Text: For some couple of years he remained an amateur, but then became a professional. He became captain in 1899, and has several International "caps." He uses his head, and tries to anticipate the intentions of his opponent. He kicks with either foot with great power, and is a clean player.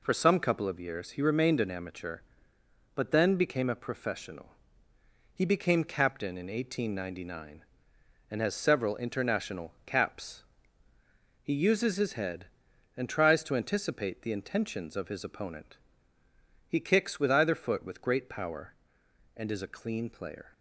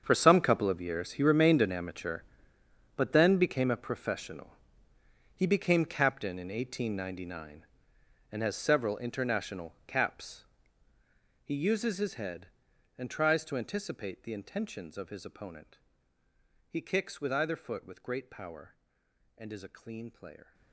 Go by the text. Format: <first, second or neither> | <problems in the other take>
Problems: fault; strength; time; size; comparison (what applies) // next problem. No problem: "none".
first | gets quieter; strong; throughout; 16 dB